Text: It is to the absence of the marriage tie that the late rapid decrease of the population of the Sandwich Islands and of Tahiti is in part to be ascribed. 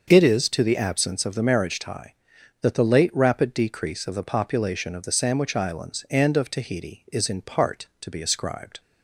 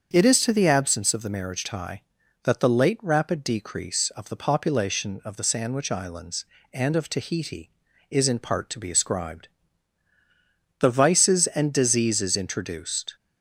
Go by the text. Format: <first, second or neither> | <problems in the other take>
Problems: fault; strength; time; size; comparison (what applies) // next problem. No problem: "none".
first | starts louder than the rest; until 1.1 s; 7 dB; also in the first // goes on to say "The vices and diseases introduced"; strong; from 10.7 s on; 2.3 s long